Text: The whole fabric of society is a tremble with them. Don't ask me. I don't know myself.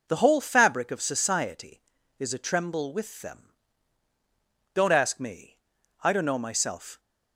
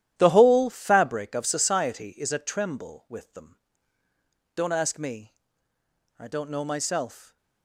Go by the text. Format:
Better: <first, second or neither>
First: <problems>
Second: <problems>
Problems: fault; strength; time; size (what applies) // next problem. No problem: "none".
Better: first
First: none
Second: gets quieter; strong; throughout; 13 dB